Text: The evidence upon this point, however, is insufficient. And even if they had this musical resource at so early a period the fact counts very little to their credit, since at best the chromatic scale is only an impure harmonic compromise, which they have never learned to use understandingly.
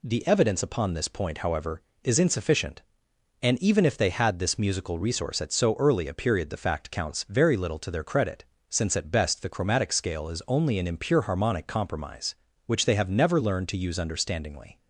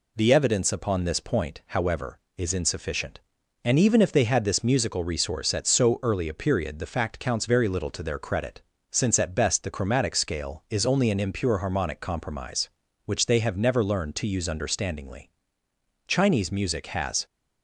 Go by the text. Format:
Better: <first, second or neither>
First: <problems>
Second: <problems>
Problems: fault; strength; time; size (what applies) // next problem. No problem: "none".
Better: first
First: none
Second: goes on to say "Chinese music has"; noticeable; from 16.0 s on; 1.1 s long